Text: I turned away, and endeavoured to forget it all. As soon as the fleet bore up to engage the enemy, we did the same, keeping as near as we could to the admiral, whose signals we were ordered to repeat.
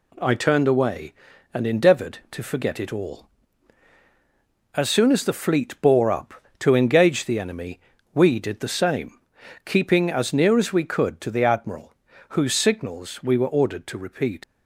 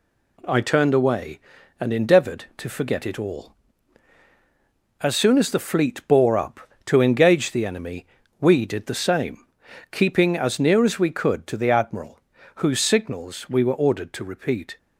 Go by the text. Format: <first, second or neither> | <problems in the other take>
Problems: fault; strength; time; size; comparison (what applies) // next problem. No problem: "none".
second | leaves "repeat" unfinished; at 14.4 s; 75 ms